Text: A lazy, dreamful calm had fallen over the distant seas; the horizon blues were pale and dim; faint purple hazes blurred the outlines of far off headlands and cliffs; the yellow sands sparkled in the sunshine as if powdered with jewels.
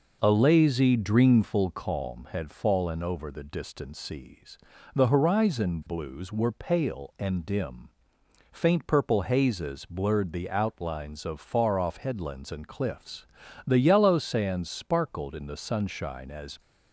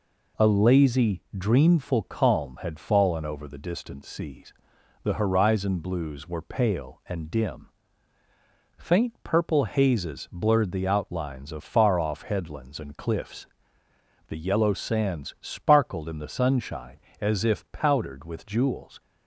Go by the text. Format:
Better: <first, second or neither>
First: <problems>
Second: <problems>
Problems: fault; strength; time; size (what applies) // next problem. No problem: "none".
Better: second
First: stops before "if powdered with jewels"; at 16.5 s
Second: none